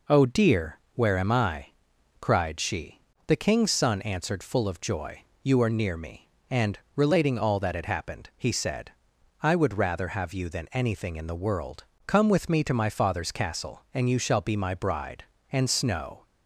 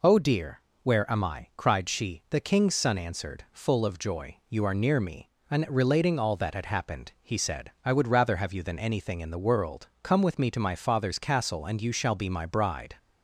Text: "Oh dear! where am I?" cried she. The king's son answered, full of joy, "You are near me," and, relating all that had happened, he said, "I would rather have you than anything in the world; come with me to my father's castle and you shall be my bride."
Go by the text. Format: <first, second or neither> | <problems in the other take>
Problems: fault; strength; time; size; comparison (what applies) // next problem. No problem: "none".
second | goes on to say "And Snow"; noticeable; from 15.5 s on; 0.72 s long